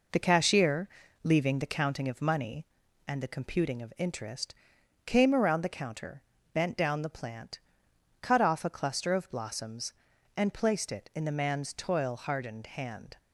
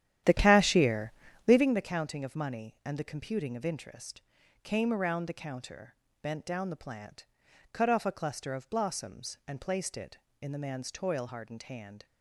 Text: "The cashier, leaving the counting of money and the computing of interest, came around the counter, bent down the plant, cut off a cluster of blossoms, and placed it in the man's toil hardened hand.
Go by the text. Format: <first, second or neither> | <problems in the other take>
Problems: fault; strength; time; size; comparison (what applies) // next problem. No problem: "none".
first | starts louder than the rest; strong; until 1.8 s; 11 dB